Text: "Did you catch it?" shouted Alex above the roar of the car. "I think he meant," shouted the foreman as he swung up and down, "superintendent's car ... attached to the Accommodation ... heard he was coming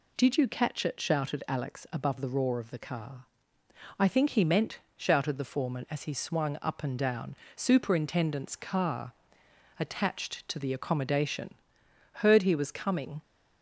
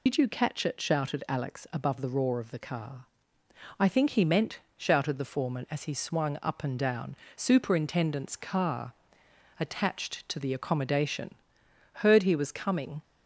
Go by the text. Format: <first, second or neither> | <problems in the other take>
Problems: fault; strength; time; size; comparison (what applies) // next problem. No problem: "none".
first | loses the start of "Did"; at 0.0 s; 100 ms